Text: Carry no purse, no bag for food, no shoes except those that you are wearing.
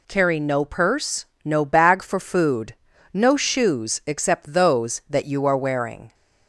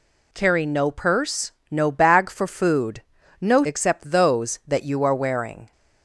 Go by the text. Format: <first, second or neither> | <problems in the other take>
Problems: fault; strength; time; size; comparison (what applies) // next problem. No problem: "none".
first | skips "shoes"; at 3.6 s